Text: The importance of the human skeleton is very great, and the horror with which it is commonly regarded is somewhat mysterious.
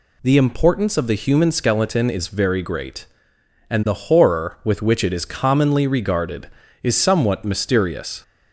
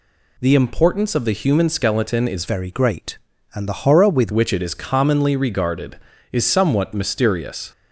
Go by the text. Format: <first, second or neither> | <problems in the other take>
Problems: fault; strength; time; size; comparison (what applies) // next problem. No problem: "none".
first | changes voice from "very" to "with"; from 2.4 to 4.3 s; 1.9 s long